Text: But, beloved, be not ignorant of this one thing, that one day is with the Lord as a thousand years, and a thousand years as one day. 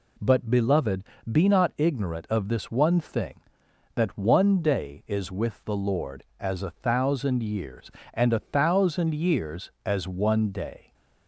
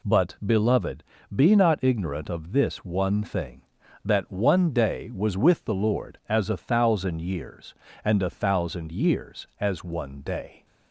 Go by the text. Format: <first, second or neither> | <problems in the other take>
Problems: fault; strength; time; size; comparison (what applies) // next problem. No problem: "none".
first | says "was" for "is"; at 5.1 s